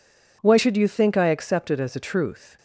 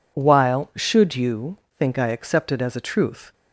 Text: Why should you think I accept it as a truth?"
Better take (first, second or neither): first